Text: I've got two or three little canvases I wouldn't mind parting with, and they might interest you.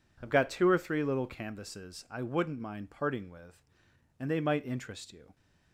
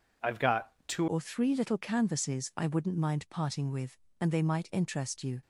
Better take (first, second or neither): first